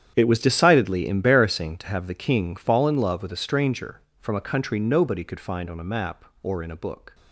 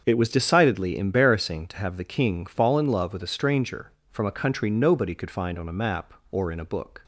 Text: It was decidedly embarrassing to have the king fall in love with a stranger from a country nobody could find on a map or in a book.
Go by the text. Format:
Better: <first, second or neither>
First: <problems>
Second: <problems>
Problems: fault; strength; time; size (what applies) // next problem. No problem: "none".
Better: second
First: gets quieter; strong; throughout; 15 dB // starts louder than the rest; strong; until 1.1 s; 9.5 dB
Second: starts louder than the rest; until 1.0 s; 7 dB